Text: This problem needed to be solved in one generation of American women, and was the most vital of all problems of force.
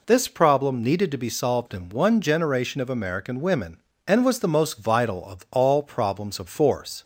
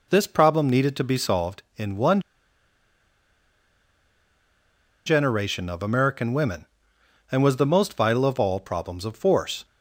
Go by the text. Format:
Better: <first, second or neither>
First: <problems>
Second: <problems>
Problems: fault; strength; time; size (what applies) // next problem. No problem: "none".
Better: first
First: none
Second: pauses between "one" and "generation"; strong; at 2.1 s; 2.8 s long